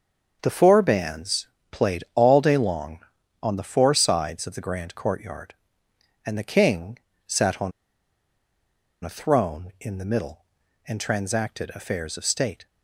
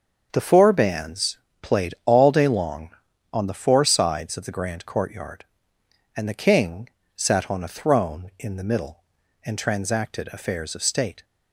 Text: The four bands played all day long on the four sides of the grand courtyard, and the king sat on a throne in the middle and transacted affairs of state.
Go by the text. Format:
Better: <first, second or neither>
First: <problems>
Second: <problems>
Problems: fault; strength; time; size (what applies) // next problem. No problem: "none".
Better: second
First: starts louder than the rest; until 1.4 s; 7 dB // pauses between "bands" and "played"; slight; at 1.4 s; 0.22 s long // pauses between "king" and "sat"; slight; at 6.9 s; 0.30 s long // pauses between "on" and "a"; strong; at 7.7 s; 1.3 s long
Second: starts louder than the rest; until 1.3 s; 7 dB // pauses between "bands" and "played"; slight; at 1.3 s; 0.22 s long // pauses between "king" and "sat"; slight; at 6.8 s; 0.28 s long